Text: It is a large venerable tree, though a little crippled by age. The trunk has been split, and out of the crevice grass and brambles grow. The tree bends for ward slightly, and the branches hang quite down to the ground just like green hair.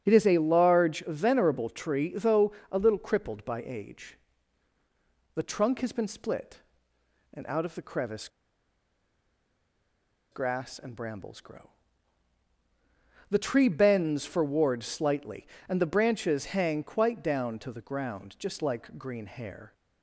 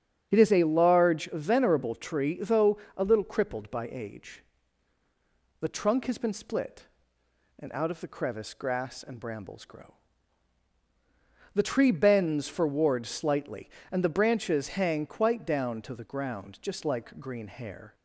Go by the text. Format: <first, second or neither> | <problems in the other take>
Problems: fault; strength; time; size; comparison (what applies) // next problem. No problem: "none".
second | starts louder than the rest; strong; until 1.0 s; 8.5 dB; strong in the second // pauses between "though" and "a"; slight; at 2.5 s; 0.20 s long; slight in the second // pauses between "crevice" and "grass"; strong; at 8.2 s; 2.0 s long